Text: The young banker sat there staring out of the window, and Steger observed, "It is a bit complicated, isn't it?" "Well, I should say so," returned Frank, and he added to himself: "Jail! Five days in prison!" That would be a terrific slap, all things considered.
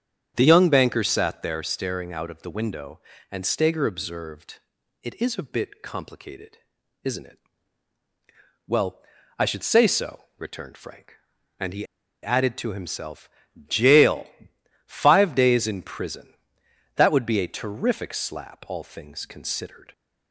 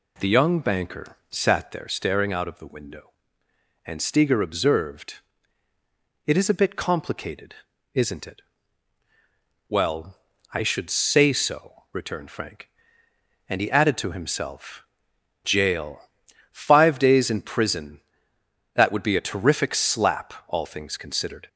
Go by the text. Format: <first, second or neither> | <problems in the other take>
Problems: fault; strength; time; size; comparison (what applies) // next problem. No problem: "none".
second | starts louder than the rest; strong; until 1.3 s; 8.5 dB // pauses between "he" and "added"; at 11.8 s; 0.37 s long